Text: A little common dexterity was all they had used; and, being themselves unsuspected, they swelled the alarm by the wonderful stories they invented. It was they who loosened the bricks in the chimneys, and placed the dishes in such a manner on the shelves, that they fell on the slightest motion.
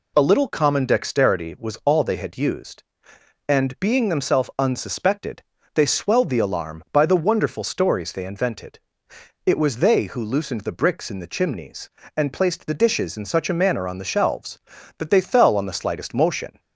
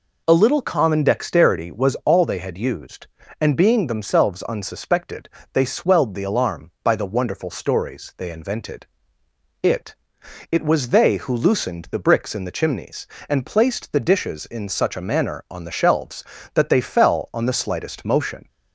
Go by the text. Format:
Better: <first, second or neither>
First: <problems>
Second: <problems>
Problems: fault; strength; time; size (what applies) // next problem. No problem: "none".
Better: first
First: none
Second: says "It" twice; at 10.4 s